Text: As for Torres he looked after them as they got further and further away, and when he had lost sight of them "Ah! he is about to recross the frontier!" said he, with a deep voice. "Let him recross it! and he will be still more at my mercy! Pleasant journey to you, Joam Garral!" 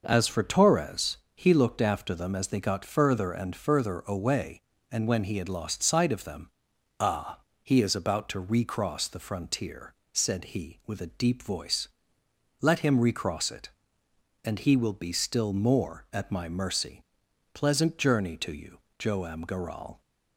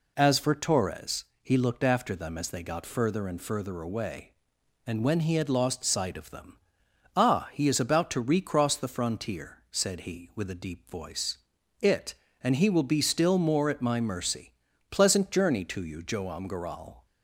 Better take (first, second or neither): first